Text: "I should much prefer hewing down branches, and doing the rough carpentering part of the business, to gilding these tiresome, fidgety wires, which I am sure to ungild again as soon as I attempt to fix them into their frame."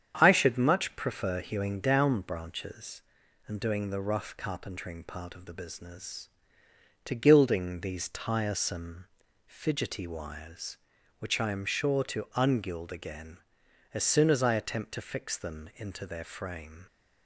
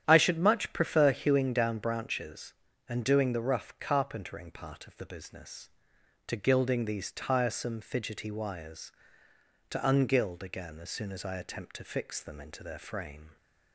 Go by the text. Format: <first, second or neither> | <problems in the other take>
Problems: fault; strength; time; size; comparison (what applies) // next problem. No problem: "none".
first | starts louder than the rest; strong; until 1.0 s; 9.5 dB; strong in the first // skips "which I am sure"; at 9.2 s